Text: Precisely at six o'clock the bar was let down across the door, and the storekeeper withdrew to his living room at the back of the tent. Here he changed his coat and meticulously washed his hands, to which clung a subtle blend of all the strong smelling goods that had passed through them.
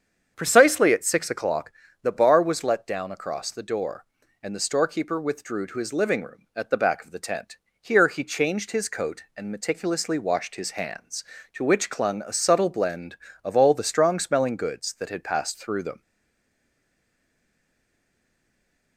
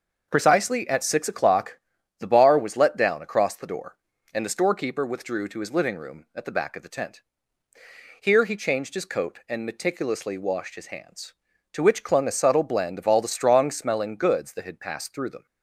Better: second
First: starts louder than the rest; strong; until 1.3 s; 7.5 dB // pauses between "o'clock" and "the"; slight; at 1.7 s; 0.32 s long // stays silent after the last word; strong; from 16.0 s on; 2.9 s long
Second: starts louder than the rest; noticeable; until 1.3 s; 6 dB // pauses between "o'clock" and "the"; at 1.7 s; 0.40 s long

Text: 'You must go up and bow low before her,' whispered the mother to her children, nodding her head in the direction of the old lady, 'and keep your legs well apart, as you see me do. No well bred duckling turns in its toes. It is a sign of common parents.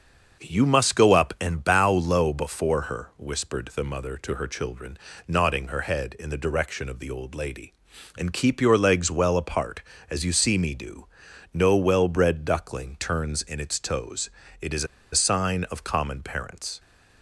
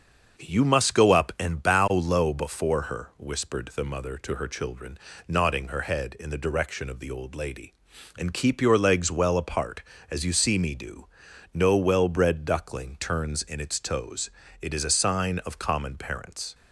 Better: second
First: starts louder than the rest; until 1.4 s; 6.5 dB // pauses between "is" and "a"; slight; at 14.8 s; 0.28 s long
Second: starts louder than the rest; until 1.4 s; 6.5 dB

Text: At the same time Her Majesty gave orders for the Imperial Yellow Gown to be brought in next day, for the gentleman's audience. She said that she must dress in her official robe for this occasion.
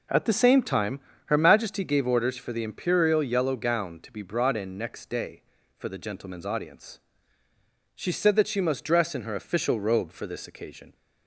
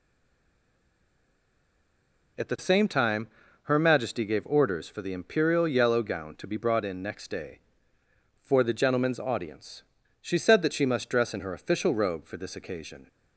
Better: first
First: pauses between "time" and "Her"; slight; at 0.9 s; 0.26 s long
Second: stays silent before the first word; until 2.3 s; 2.3 s long // pauses between "time" and "Her"; slight; at 3.2 s; 0.36 s long

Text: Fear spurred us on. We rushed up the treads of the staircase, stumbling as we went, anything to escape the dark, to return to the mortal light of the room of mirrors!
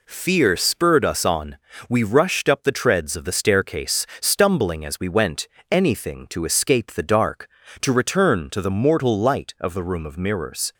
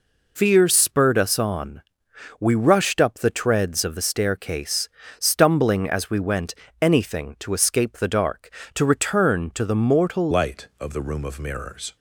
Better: first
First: none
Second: changes voice at "light"; from 10.3 s on; 1.6 s long

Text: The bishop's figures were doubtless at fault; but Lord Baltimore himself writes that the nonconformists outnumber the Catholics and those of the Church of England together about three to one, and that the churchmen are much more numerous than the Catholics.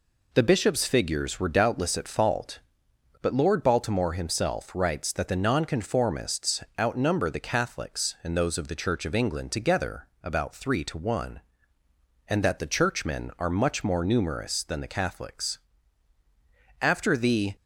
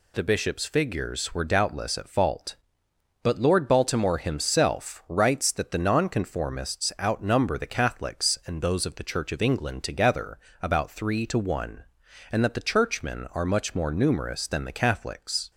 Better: second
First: pauses between "nonconformists" and "outnumber"; slight; at 6.6 s; 0.16 s long // pauses between "together" and "about"; slight; at 10.0 s; 0.16 s long // goes on to say "After the"; noticeable; from 16.8 s on; 0.74 s long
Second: pauses between "together" and "about"; slight; at 10.3 s; 0.24 s long

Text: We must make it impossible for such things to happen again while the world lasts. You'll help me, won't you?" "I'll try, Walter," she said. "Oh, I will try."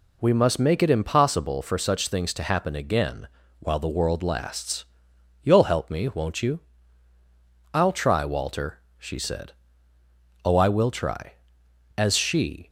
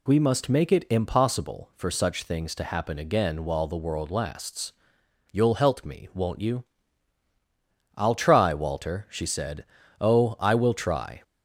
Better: second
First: pauses between "again" and "while"; slight; at 3.2 s; 0.32 s long // goes on to say "As she"; noticeable; from 11.9 s on; 0.72 s long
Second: none

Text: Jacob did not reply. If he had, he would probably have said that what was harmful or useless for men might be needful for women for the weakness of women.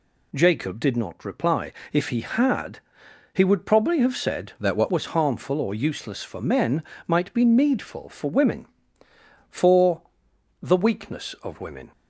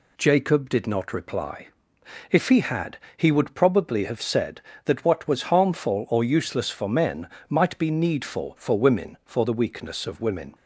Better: second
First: changes voice from "that" to "what"; from 4.5 to 4.9 s; 0.4 s long // pauses between "men" and "might"; slight; at 6.8 s; 0.24 s long // pauses between "for" and "the"; noticeable; at 10.0 s; 0.62 s long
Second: pauses between "men" and "might"; slight; at 7.2 s; 0.22 s long

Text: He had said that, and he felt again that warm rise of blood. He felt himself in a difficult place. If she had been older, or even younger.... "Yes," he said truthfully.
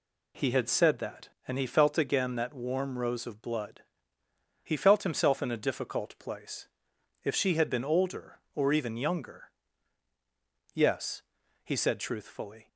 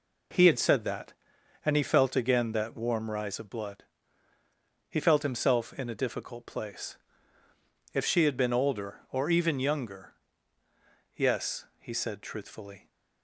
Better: second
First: says "rose" for "rise"; at 2.9 s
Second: none

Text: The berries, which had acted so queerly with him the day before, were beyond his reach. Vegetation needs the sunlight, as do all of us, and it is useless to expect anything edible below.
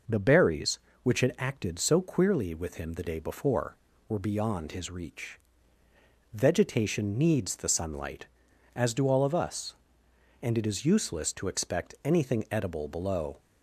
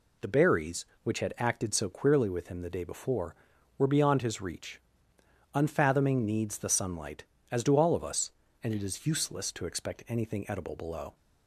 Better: first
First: none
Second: says "Unfathoming" for "Vegetation"; at 5.5 s

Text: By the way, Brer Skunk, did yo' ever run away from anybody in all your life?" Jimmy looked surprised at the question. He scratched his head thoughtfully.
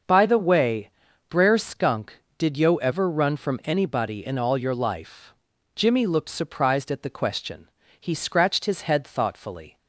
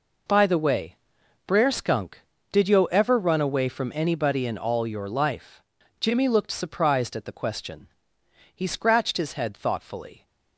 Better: second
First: starts louder than the rest; noticeable; until 1.4 s; 6 dB // skips "away"; at 3.3 s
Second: none

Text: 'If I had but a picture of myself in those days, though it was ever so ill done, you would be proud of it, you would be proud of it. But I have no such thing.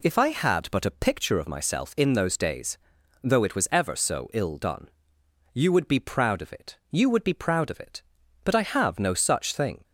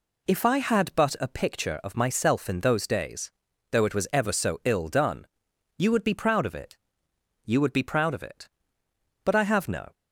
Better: first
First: none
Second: stops before "such thing"; at 9.9 s

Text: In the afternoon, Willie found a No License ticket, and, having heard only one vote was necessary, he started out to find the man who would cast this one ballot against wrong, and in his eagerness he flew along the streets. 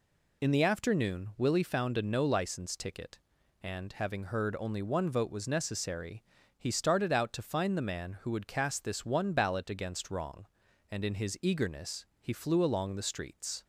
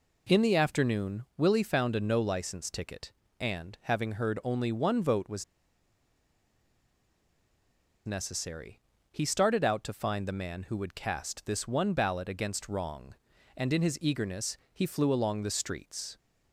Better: first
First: pauses between "eagerness" and "he"; slight; at 12.0 s; 0.16 s long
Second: pauses between "was" and "necessary"; strong; at 5.4 s; 2.6 s long // pauses between "eagerness" and "he"; slight; at 14.5 s; 0.16 s long

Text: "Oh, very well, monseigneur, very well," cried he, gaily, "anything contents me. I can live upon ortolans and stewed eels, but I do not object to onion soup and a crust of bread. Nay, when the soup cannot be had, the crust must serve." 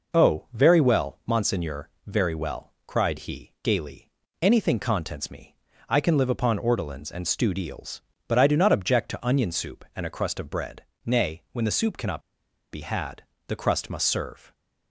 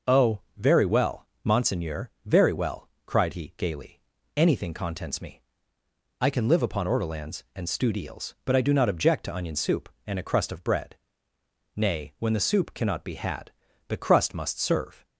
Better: second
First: pauses between "cannot" and "be"; noticeable; at 12.1 s; 0.51 s long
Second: none

